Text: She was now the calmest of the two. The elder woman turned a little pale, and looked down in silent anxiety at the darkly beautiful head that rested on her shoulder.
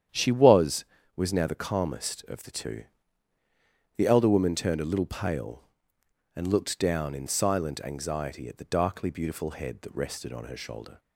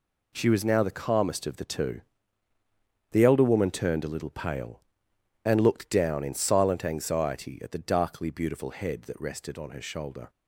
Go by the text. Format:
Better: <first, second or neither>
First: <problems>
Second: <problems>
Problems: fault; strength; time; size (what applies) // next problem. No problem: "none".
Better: second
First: starts louder than the rest; strong; until 1.4 s; 9.5 dB // says "was" twice; at 1.1 s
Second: none